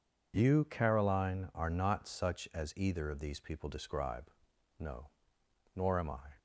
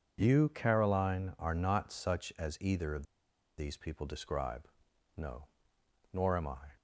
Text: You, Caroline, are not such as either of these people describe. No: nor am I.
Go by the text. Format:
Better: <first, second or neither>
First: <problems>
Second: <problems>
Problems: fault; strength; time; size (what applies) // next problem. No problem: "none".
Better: first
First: none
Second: pauses between "of" and "these"; noticeable; at 3.0 s; 0.52 s long